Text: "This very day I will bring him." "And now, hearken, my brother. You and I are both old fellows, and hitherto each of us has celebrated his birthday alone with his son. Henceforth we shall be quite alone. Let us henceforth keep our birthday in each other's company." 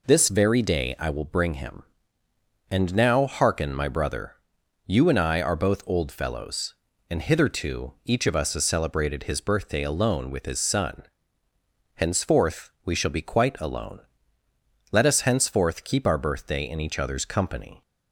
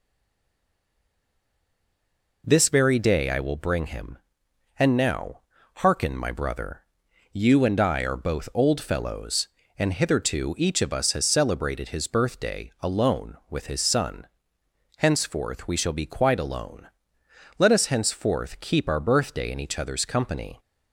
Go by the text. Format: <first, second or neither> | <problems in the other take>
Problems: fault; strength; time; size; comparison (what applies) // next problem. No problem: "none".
first | stays silent before the first word; until 2.4 s; 2.4 s long